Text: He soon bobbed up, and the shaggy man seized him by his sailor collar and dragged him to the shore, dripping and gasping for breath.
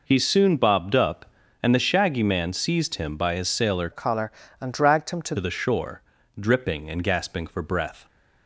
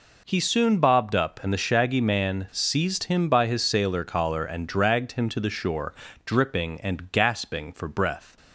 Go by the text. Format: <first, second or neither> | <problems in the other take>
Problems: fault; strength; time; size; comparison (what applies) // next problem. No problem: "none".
second | changes voice from "collar" to "to"; from 3.9 to 5.3 s; 1.4 s long